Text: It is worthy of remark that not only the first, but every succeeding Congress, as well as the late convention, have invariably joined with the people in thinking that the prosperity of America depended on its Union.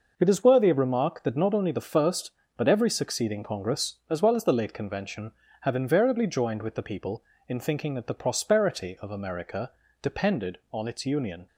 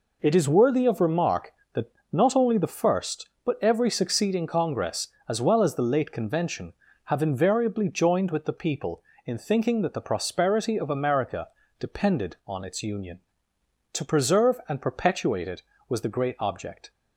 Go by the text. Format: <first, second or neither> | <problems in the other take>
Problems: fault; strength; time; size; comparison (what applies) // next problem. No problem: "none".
first | pauses between "that" and "not"; slight; at 1.9 s; 0.22 s long // pauses between "America" and "depended"; slight; at 11.4 s; 0.30 s long; slight in the first // goes on to say "To preserve and perpetuate it was the great object"; strong; from 13.9 s on; 2.9 s long